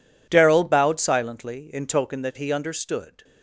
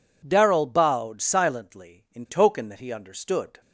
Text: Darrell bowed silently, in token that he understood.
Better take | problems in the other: neither | none

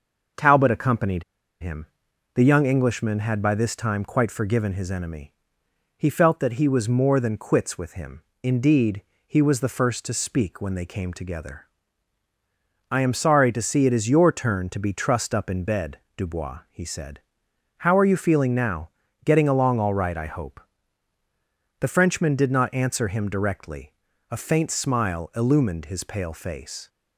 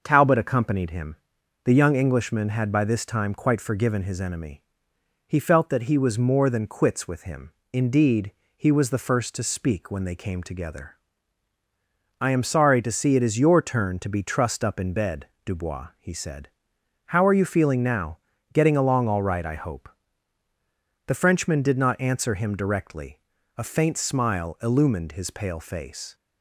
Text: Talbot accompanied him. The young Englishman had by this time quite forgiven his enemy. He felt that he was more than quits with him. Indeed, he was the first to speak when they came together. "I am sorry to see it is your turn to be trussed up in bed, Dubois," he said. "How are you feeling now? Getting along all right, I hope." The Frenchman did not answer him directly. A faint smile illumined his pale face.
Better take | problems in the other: second | starts louder than the rest; noticeable; until 1.7 s; 6 dB; noticeable in the second // pauses between "accompanied" and "him"; at 1.2 s; 0.37 s long

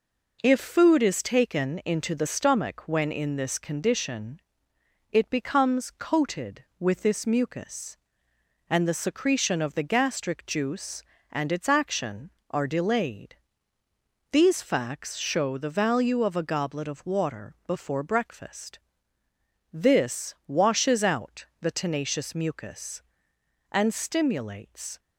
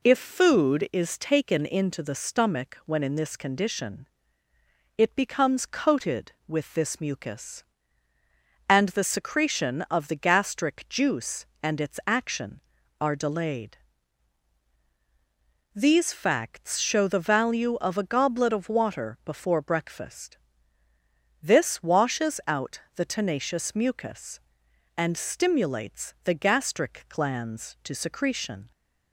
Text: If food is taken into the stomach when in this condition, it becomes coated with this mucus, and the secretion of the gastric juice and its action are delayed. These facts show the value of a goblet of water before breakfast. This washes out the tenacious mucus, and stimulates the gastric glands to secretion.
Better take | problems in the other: second | stops before "the gastric glands to secretion"; at 24.9 s

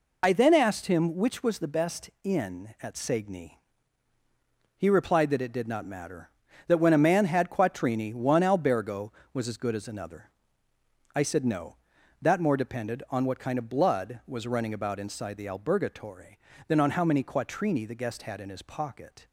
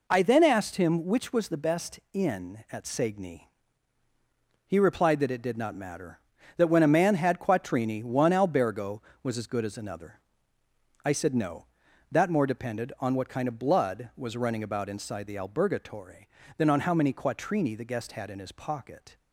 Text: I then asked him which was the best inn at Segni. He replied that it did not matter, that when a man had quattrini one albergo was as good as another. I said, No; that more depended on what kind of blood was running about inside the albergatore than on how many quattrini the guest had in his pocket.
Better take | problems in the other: second | loses the start of "I"; at 0.2 s; 35 ms

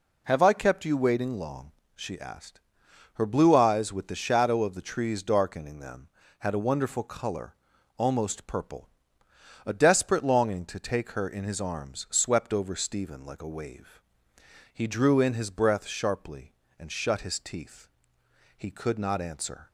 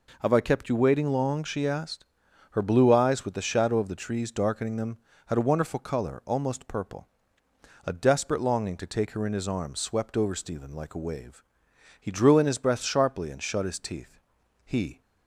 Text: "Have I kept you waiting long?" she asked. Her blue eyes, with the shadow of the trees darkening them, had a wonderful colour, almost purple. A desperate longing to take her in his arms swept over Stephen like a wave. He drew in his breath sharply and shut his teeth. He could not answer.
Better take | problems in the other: first | stops before "could not answer"; at 15.0 s

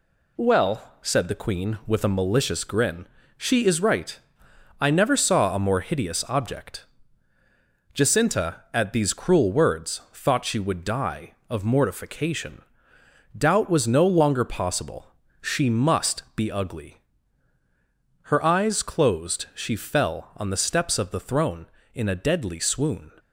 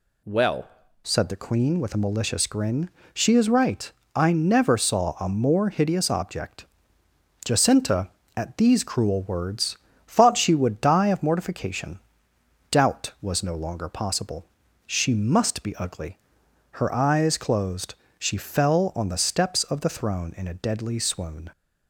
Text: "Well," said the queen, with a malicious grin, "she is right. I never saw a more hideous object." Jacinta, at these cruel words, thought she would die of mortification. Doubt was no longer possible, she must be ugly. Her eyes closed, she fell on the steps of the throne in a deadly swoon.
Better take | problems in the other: first | changes voice at "said"; from 1.0 s on; 20.4 s long

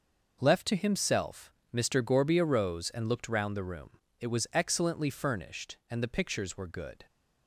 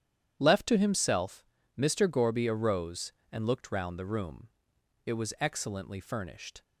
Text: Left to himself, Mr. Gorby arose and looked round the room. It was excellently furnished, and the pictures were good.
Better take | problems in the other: first | starts louder than the rest; strong; until 1.4 s; 10 dB // stops before "and the pictures were good"; at 6.6 s

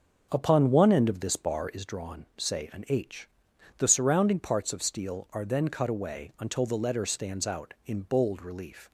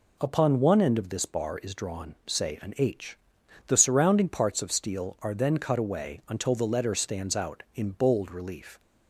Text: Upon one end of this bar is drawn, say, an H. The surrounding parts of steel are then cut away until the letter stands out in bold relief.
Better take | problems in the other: second | starts louder than the rest; until 1.8 s; 7 dB

